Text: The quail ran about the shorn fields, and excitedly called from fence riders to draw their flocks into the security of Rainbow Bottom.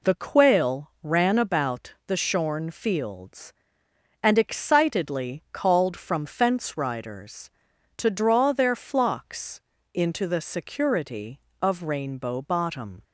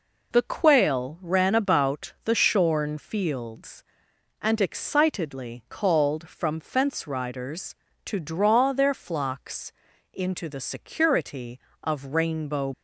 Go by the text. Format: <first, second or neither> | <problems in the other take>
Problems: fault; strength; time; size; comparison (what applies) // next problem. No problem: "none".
first | pauses between "flocks" and "into"; at 9.7 s; 0.40 s long; slight in the first // stops before "Bottom"; at 12.7 s